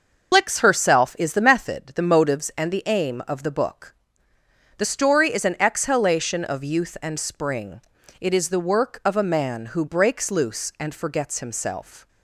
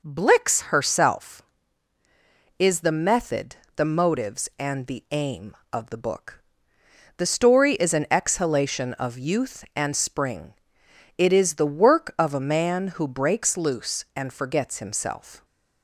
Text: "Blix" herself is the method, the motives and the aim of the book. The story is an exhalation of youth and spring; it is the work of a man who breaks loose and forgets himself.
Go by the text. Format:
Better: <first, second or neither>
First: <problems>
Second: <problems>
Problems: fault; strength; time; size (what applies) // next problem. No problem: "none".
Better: second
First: loses the start of "Blix"; at 0.3 s; 45 ms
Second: none